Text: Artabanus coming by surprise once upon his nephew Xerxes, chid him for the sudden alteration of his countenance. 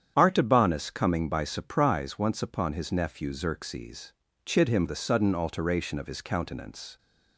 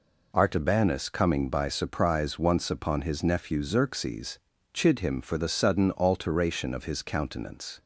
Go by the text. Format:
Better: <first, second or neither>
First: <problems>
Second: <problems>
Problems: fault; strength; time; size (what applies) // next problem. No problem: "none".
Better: second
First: starts louder than the rest; strong; until 1.1 s; 9 dB // skips "for"; at 4.8 s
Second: none